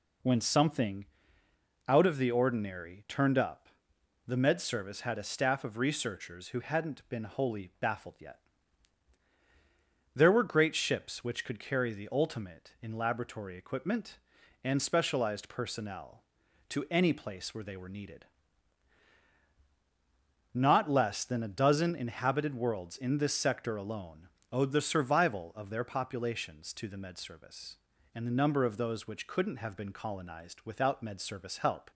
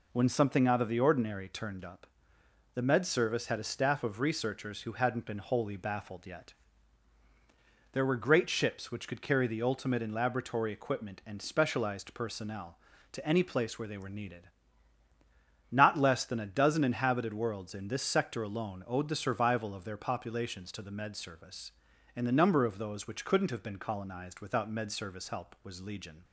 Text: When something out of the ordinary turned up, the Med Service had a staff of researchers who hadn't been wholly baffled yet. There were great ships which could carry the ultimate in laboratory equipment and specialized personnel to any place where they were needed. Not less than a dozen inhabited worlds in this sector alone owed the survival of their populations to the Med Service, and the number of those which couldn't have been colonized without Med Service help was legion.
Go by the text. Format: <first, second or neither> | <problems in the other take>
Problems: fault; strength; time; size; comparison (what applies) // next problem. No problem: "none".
second | pauses between "something" and "out"; noticeable; at 1.0 s; 0.82 s long // pauses between "alone" and "owed"; slight; at 24.2 s; 0.24 s long // stops before "was legion"; at 31.9 s